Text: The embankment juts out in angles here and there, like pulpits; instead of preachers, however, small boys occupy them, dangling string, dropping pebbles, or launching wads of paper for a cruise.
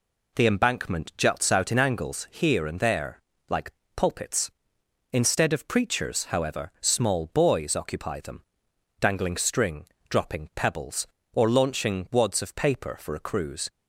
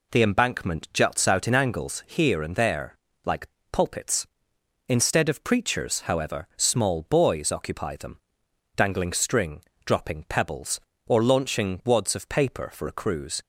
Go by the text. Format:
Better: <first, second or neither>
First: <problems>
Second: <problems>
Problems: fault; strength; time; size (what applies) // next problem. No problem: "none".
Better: neither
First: pauses between "like" and "pulpits"; slight; at 3.7 s; 0.24 s long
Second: pauses between "like" and "pulpits"; slight; at 3.4 s; 0.24 s long